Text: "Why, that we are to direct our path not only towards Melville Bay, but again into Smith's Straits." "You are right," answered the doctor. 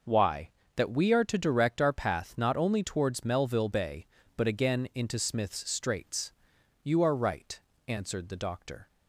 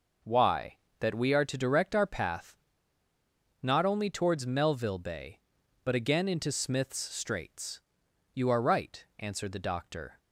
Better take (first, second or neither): first